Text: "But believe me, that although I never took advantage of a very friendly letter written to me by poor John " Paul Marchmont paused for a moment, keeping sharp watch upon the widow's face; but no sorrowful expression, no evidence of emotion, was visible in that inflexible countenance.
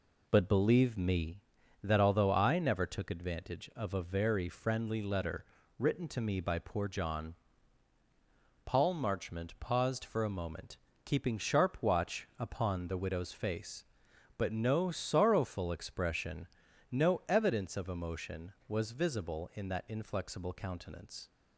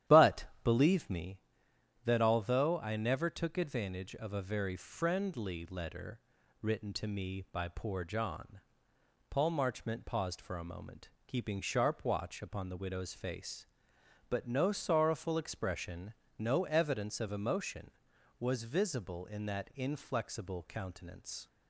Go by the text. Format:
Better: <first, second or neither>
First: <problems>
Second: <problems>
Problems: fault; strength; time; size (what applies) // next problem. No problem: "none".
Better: first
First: pauses between "letter" and "written"; slight; at 5.4 s; 0.34 s long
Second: starts louder than the rest; strong; until 1.3 s; 12 dB // pauses between "But" and "believe"; slight; at 0.4 s; 0.18 s long // pauses between "letter" and "written"; at 6.1 s; 0.42 s long